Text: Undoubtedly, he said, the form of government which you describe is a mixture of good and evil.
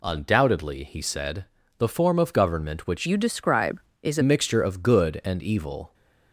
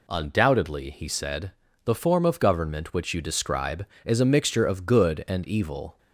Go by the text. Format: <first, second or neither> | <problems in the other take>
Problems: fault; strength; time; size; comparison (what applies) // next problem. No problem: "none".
second | changes voice from "you" to "a"; from 3.0 to 4.2 s; 1.2 s long